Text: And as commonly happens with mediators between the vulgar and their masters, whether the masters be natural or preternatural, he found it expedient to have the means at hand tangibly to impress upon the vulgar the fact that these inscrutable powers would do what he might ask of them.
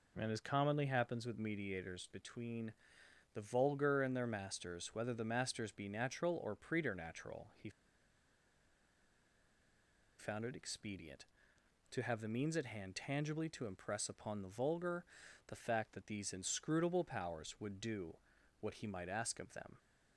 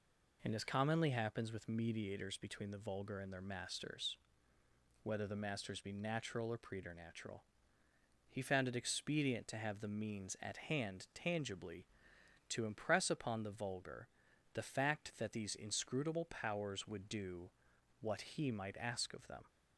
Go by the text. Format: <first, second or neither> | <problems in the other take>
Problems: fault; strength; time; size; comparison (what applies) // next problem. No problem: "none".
second | pauses between "between" and "the"; noticeable; at 2.7 s; 0.60 s long // pauses between "he" and "found"; strong; at 7.6 s; 2.4 s long // pauses between "vulgar" and "the"; at 15.0 s; 0.44 s long; noticeable in the second // pauses between "do" and "what"; at 18.1 s; 0.44 s long; noticeable in the second